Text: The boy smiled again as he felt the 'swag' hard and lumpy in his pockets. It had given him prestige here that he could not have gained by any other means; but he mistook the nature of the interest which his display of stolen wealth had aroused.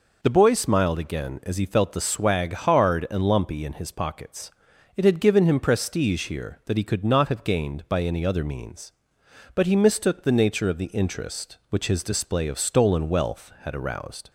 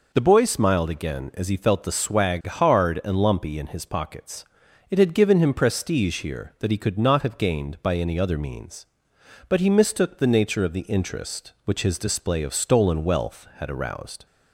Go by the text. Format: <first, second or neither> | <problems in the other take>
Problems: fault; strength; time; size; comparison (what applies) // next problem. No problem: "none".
neither | none